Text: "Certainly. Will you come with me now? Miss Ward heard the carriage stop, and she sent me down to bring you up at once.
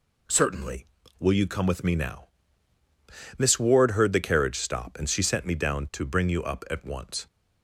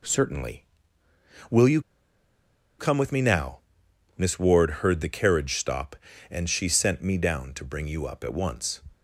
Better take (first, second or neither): first